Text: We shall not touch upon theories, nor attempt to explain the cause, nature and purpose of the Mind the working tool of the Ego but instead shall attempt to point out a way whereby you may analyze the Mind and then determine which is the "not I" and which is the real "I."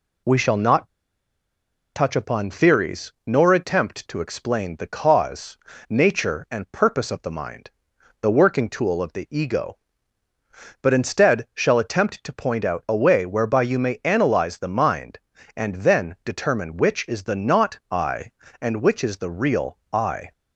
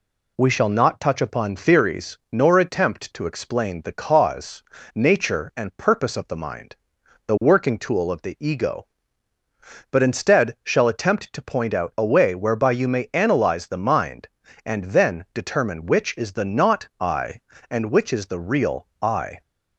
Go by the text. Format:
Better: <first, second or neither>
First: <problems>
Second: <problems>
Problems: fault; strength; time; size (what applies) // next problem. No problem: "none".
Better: second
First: pauses between "not" and "touch"; at 0.8 s; 1.0 s long // pauses between "Mind" and "the"; noticeable; at 7.6 s; 0.50 s long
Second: pauses between "Mind" and "the"; noticeable; at 6.7 s; 0.50 s long